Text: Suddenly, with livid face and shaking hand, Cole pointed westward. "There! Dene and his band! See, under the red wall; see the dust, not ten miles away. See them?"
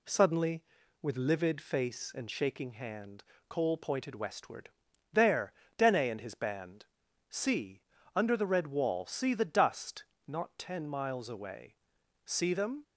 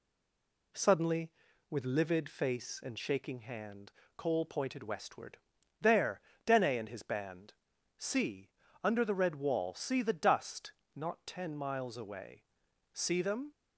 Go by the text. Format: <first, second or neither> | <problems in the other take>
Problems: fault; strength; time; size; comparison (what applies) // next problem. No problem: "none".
first | stays silent before the first word; slight; until 0.7 s; 0.7 s long